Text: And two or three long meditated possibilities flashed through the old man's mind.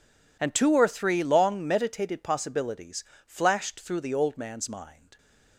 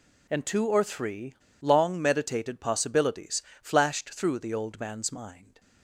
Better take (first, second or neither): first